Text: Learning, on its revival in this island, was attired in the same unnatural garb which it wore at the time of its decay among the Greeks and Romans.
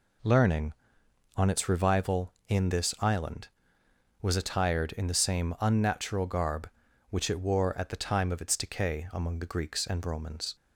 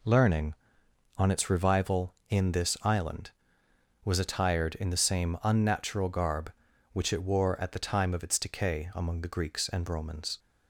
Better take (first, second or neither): neither